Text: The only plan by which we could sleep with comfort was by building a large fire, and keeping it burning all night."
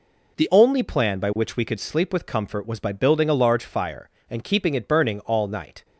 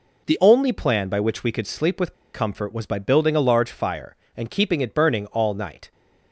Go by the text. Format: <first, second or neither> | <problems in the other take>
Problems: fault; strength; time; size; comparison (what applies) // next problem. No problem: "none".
first | pauses between "with" and "comfort"; slight; at 2.1 s; 0.20 s long